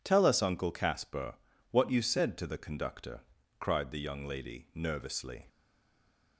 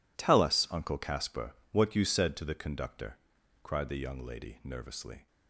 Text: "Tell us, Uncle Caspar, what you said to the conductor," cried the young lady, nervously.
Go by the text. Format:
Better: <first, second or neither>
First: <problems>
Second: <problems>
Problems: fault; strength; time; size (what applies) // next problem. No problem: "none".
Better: second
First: stays silent after the last word; slight; from 5.4 s on; 0.9 s long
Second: none